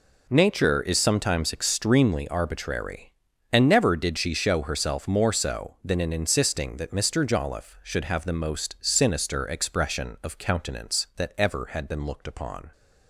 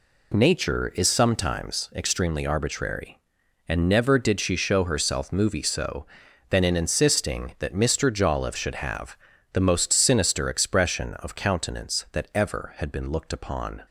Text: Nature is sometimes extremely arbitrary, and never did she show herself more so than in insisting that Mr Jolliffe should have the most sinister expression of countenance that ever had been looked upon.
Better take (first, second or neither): first